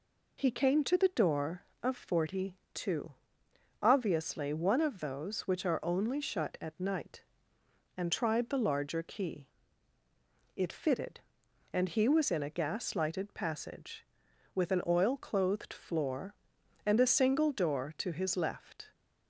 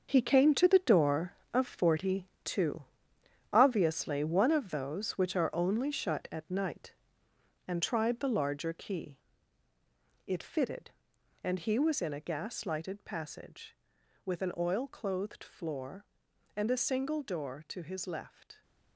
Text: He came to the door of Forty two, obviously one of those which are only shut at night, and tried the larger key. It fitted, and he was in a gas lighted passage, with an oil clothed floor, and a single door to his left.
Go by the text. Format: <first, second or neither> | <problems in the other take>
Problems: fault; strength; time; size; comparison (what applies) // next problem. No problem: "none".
first | gets quieter; strong; throughout; 10.5 dB // pauses between "Forty" and "two"; slight; at 2.2 s; 0.16 s long; slight in the first